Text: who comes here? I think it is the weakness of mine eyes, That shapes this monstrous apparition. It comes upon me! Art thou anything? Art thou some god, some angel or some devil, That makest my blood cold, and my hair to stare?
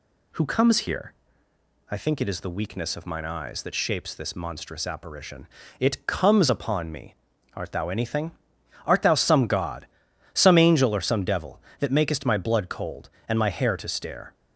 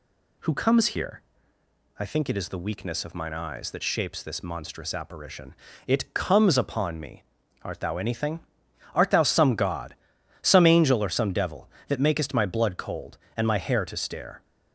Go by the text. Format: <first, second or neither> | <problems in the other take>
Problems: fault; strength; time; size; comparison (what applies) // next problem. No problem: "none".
neither | none